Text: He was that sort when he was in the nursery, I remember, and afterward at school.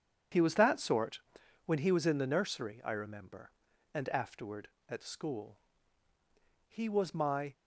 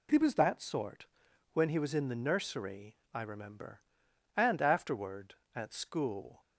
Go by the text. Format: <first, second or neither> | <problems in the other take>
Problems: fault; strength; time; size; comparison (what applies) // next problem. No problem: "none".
second | pauses between "sort" and "when"; noticeable; at 1.1 s; 0.48 s long; noticeable in the second // goes on to say "He was my"; noticeable; from 6.6 s on; 0.86 s long